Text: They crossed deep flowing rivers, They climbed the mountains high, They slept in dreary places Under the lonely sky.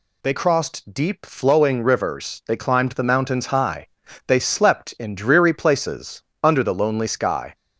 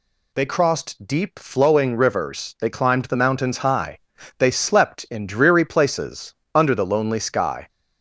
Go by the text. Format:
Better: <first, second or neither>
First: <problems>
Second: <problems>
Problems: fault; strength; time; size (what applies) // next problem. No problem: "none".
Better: neither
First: pauses between "places" and "Under"; slight; at 6.2 s; 0.18 s long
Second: pauses between "places" and "Under"; slight; at 6.3 s; 0.18 s long